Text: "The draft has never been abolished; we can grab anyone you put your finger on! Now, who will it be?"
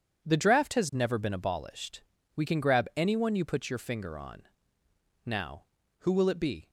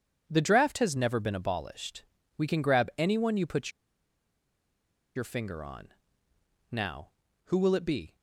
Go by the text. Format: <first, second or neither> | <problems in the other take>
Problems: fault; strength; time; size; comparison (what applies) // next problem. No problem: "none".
first | pauses between "put" and "your"; strong; at 3.7 s; 1.4 s long